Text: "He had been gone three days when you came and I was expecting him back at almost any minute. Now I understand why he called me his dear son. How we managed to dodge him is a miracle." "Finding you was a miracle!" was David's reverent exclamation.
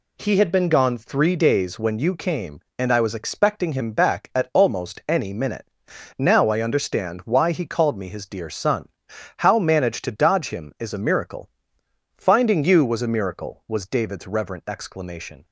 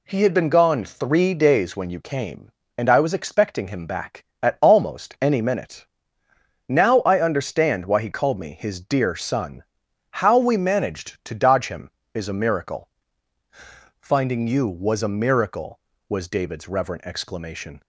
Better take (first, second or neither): second